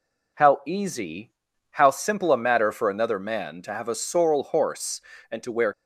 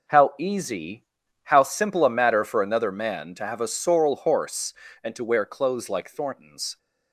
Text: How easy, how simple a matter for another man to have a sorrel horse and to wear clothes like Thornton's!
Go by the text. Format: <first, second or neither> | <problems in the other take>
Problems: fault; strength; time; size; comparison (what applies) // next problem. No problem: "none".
second | stops before "clothes like Thornton's"; at 5.7 s